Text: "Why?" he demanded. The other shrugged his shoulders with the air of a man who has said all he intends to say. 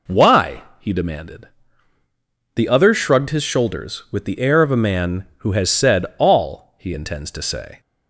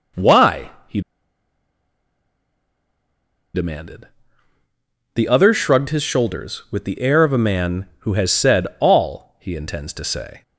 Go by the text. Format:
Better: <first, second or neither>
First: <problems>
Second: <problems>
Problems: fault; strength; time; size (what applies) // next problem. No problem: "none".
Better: first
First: none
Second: pauses between "he" and "demanded"; strong; at 1.0 s; 2.5 s long